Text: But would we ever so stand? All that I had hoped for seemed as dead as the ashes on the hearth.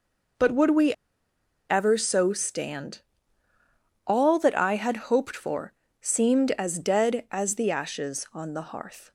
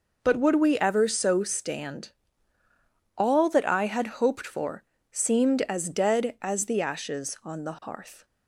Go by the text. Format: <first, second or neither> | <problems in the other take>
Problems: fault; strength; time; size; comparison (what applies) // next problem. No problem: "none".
second | pauses between "we" and "ever"; noticeable; at 0.9 s; 0.76 s long // pauses between "for" and "seemed"; slight; at 5.7 s; 0.26 s long; slight in the second